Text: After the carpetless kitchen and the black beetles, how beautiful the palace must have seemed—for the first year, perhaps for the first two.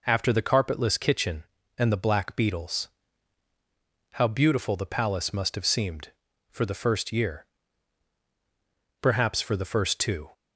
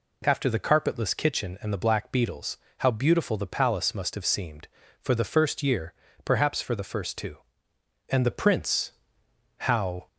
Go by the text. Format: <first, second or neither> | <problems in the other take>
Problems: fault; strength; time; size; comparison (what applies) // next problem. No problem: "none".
first | goes on to say "And the Prince how"; strong; from 8.0 s on; 1.9 s long